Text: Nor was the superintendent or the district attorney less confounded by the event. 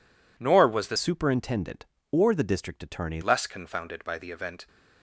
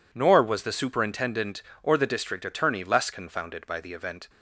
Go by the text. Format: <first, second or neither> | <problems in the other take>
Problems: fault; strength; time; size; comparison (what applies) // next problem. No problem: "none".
second | changes voice from "superintendent" to "attorney"; from 0.9 to 3.2 s; 2.3 s long